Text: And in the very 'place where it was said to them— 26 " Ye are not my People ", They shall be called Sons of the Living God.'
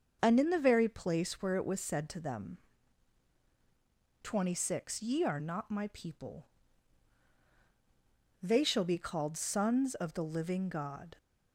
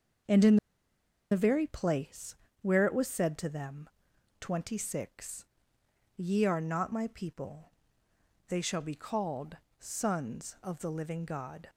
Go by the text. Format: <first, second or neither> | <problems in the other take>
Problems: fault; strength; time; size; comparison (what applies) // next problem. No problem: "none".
first | starts louder than the rest; until 2.0 s; 7 dB; also in the first // pauses between "in" and "the"; noticeable; at 0.5 s; 0.75 s long // pauses between "place" and "where"; slight; at 2.3 s; 0.28 s long // pauses between "called" and "Sons"; slight; at 9.5 s; 0.20 s long